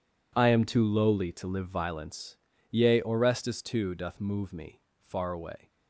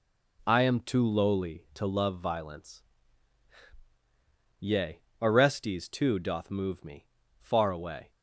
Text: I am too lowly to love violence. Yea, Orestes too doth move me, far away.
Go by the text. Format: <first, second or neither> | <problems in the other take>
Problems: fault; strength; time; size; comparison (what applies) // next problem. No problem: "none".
second | says "live" for "love"; at 1.4 s